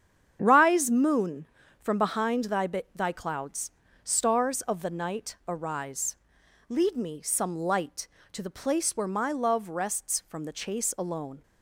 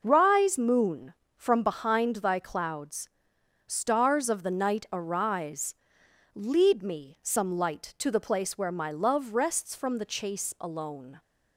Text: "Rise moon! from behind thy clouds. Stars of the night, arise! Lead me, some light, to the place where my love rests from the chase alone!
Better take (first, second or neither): second